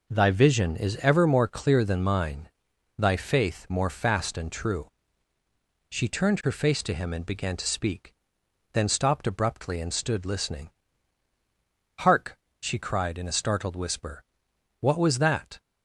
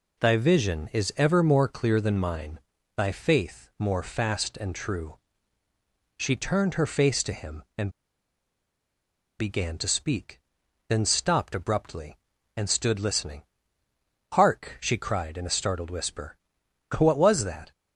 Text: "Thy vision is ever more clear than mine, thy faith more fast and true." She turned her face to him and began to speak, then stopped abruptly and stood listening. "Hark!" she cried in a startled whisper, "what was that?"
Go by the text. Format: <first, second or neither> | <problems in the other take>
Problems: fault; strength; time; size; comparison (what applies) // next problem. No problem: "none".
first | pauses between "and" and "began"; strong; at 7.9 s; 1.4 s long